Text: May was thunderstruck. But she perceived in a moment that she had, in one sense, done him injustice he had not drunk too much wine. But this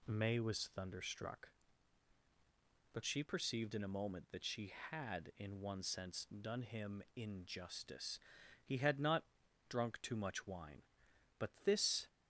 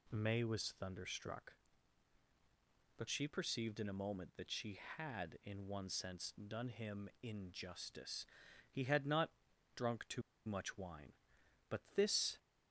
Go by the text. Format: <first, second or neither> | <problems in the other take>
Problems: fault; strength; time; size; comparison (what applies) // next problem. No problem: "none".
first | pauses between "injustice" and "he"; at 8.2 s; 0.44 s long; also in the first // pauses between "not" and "drunk"; at 9.2 s; 0.44 s long; also in the first // pauses between "too" and "much"; slight; at 10.2 s; 0.24 s long // pauses between "But" and "this"; slight; at 11.7 s; 0.16 s long; slight in the first